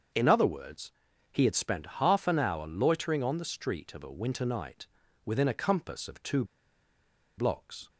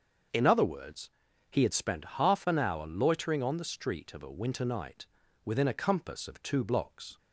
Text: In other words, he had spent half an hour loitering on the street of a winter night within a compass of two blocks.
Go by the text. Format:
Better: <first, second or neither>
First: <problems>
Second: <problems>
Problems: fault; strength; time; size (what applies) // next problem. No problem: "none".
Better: second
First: starts louder than the rest; until 1.5 s; 7 dB // pauses between "night" and "within"; at 4.8 s; 0.38 s long // pauses between "two" and "blocks"; noticeable; at 6.4 s; 0.93 s long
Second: starts louder than the rest; until 1.7 s; 7 dB // pauses between "night" and "within"; at 5.0 s; 0.38 s long